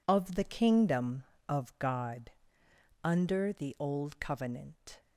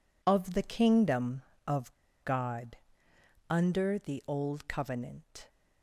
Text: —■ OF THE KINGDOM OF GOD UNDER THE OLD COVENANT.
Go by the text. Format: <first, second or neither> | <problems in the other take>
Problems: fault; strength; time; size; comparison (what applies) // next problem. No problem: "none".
first | pauses between "OF" and "GOD"; slight; at 1.9 s; 0.30 s long // pauses between "GOD" and "UNDER"; noticeable; at 2.7 s; 0.74 s long; noticeable in the first